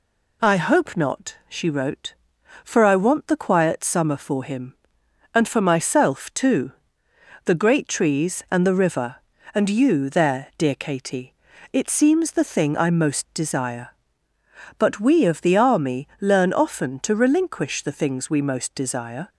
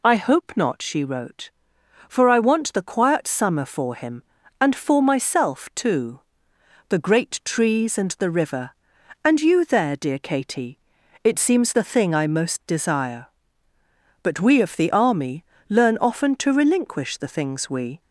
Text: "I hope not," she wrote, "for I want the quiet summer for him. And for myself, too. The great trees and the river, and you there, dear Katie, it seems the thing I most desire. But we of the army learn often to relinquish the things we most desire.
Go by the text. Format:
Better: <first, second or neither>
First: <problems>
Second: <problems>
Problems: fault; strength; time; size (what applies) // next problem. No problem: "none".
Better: first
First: none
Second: pauses between "army" and "learn"; slight; at 15.4 s; 0.24 s long // stops before "most desire"; at 18.0 s